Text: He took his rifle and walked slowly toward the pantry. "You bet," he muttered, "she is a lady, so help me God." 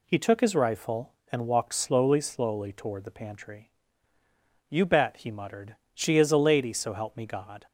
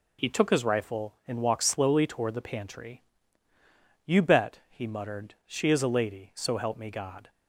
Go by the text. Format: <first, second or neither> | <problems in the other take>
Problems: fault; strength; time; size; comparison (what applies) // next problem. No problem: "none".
second | says "slowly" twice; at 2.2 s